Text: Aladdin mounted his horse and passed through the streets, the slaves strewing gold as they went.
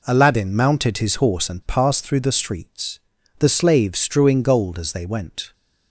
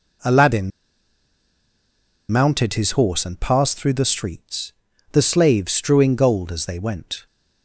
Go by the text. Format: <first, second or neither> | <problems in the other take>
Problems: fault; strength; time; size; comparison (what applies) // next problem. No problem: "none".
first | pauses between "Aladdin" and "mounted"; strong; at 0.7 s; 1.6 s long